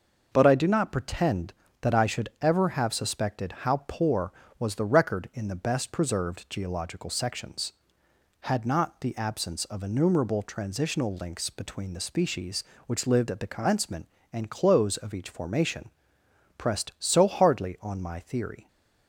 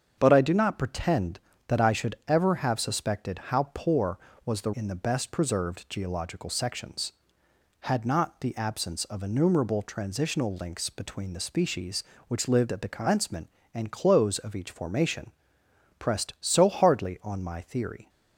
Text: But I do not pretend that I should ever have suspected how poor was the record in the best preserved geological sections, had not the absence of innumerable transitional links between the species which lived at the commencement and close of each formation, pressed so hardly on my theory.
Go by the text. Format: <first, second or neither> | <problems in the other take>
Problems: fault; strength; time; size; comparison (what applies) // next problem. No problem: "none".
first | starts louder than the rest; strong; until 1.1 s; 7.5 dB; noticeable in the first // skips "record"; at 4.7 s